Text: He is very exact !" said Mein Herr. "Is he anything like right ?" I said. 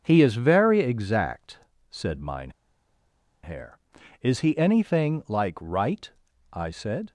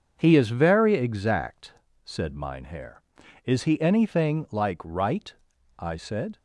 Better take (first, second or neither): second